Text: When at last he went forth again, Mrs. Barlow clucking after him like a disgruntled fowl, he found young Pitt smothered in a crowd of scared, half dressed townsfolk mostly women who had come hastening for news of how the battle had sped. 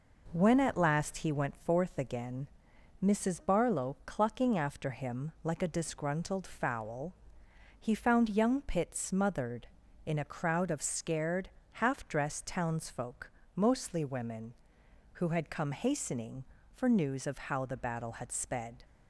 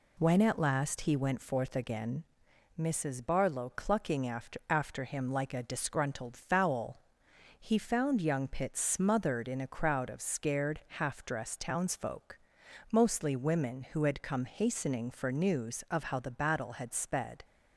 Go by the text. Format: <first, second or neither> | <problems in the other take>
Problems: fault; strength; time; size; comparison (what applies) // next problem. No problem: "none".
first | says "after" twice; at 4.6 s // pauses between "townsfolk" and "mostly"; noticeable; at 12.3 s; 0.54 s long; slight in the first